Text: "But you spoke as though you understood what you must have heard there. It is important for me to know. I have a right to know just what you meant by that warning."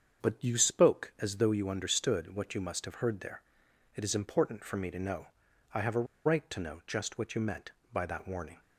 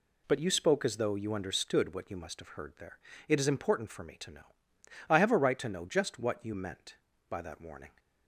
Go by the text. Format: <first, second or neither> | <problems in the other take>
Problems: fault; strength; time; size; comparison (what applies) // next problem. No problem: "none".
second | starts louder than the rest; until 1.3 s; 7 dB // pauses between "a" and "right"; slight; at 6.0 s; 0.21 s long